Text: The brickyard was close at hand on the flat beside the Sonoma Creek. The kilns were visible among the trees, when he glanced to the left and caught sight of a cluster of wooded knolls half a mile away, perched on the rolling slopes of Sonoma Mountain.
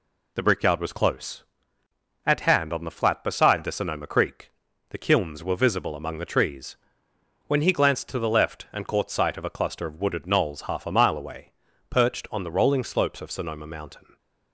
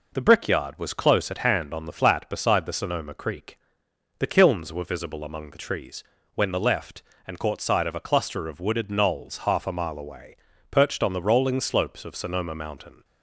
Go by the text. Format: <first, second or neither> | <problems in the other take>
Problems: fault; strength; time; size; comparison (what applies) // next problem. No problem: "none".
first | skips "he glanced to"; at 6.5 s